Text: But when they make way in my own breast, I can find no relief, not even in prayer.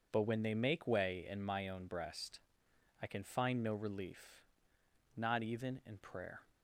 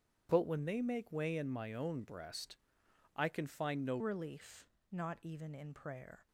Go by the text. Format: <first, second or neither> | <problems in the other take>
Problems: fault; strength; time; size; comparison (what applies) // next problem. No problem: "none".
first | starts louder than the rest; strong; until 1.3 s; 8.5 dB // changes voice at "relief"; from 3.9 s on; 2.3 s long